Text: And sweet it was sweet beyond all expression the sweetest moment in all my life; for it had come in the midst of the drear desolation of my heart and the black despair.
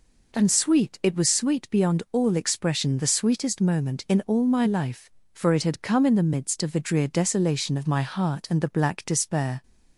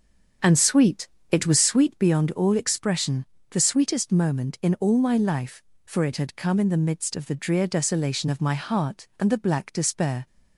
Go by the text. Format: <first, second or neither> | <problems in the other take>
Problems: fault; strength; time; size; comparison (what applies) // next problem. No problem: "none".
first | starts louder than the rest; strong; until 2.1 s; 7 dB // pauses between "sweet" and "it"; slight; at 1.0 s; 0.24 s long // pauses between "expression" and "the"; slight; at 3.2 s; 0.24 s long